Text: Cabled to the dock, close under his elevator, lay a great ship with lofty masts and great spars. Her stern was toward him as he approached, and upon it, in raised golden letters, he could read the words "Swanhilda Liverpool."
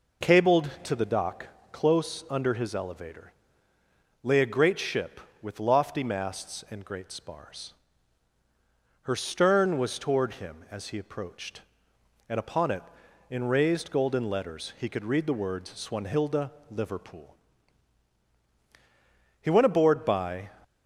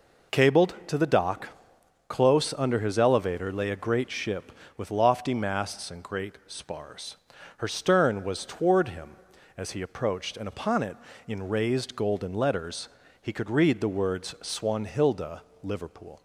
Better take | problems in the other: second | pauses between "Swanhilda" and "Liverpool"; slight; at 16.5 s; 0.18 s long; slight in the second // goes on to say "He went aboard by"; noticeable; from 19.3 s on; 1.1 s long

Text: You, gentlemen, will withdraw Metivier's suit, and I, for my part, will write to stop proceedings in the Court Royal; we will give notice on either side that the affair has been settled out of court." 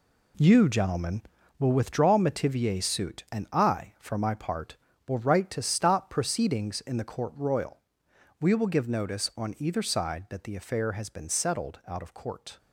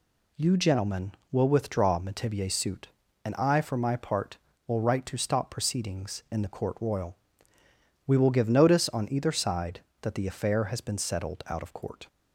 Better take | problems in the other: second | gets quieter; strong; throughout; 9 dB

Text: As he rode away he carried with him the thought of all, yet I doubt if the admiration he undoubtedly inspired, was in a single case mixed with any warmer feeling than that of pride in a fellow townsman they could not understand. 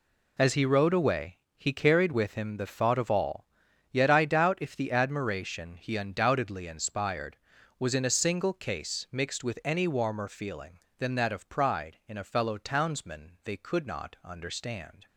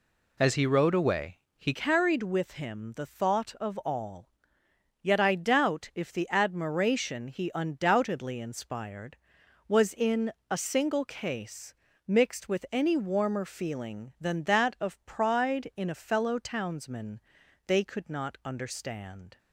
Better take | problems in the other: first | pauses between "away" and "he"; slight; at 1.3 s; 0.20 s long; slight in the first // changes voice at "carried"; from 1.7 s on; 17.6 s long // pauses between "in" and "a"; slight; at 10.3 s; 0.18 s long // pauses between "case" and "mixed"; slight; at 11.7 s; 0.34 s long // pauses between "townsman" and "they"; noticeable; at 17.1 s; 0.46 s long

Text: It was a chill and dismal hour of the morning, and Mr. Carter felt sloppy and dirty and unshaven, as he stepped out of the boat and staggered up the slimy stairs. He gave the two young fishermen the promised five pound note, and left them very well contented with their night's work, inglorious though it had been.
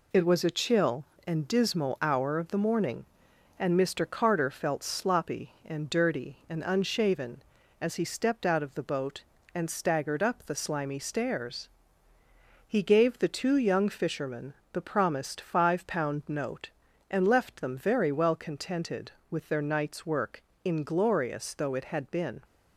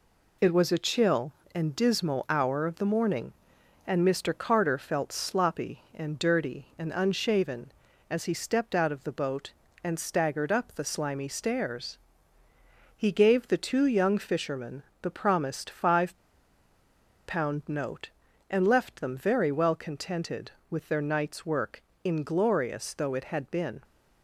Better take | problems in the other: first | pauses between "fishermen" and "the"; slight; at 14.8 s; 0.20 s long; slight in the first // pauses between "five" and "pound"; at 16.1 s; 1.1 s long

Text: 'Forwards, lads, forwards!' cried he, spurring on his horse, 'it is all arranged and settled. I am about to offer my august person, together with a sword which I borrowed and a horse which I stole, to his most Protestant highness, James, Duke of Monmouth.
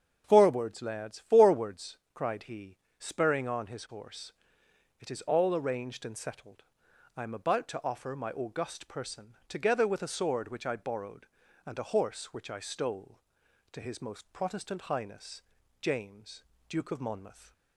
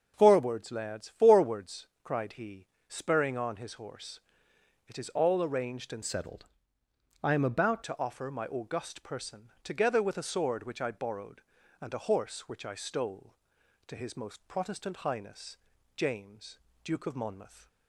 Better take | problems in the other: first | starts louder than the rest; until 1.1 s; 6.5 dB; strong in the first // changes voice from "settled" to "about"; from 6.0 to 7.8 s; 1.8 s long

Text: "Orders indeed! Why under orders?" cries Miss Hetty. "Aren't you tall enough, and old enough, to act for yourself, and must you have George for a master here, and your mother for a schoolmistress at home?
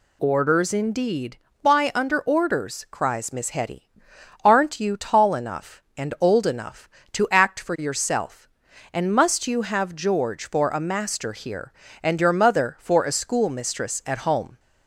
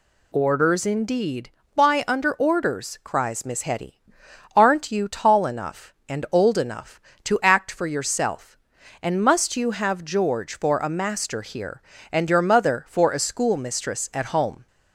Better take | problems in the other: neither | none

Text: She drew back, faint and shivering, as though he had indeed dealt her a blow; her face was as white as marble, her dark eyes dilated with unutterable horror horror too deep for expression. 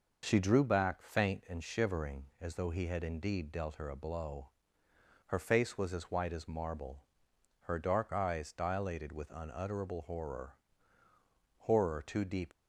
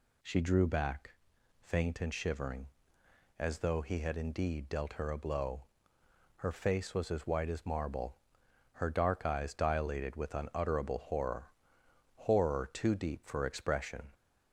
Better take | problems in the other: second | pauses between "horror" and "horror"; at 10.5 s; 1.1 s long; noticeable in the second // stops before "for expression"; at 12.5 s

